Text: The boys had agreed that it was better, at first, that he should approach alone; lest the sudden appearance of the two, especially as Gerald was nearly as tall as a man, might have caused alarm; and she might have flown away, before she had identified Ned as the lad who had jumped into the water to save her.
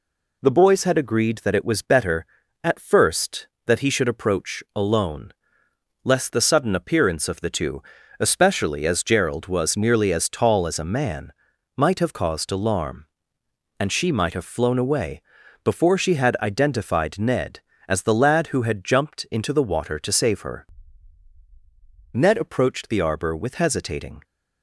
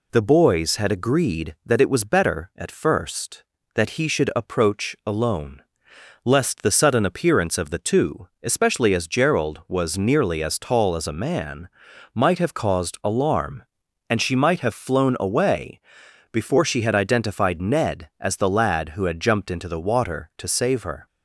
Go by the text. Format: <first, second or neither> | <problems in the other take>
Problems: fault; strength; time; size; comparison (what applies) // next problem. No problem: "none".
second | goes on to say "Ned approached the arbor with hesitating"; strong; from 22.1 s on; 2.0 s long